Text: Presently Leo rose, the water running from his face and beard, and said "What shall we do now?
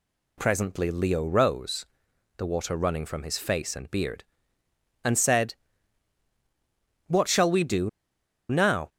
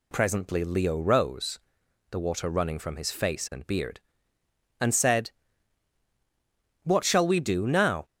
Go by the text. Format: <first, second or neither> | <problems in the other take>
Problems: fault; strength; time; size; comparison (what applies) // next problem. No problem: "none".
second | pauses between "said" and "What"; strong; at 5.5 s; 1.5 s long; strong in the second // pauses between "do" and "now"; noticeable; at 7.8 s; 0.60 s long